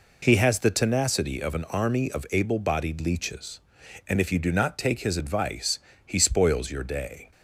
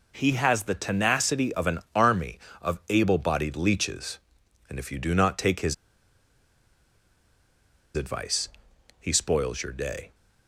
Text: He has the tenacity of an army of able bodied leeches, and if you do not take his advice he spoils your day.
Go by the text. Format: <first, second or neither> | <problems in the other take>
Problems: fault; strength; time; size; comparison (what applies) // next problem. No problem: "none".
first | pauses between "his" and "advice"; strong; at 5.7 s; 2.2 s long // pauses between "advice" and "he"; noticeable; at 8.4 s; 0.50 s long; slight in the first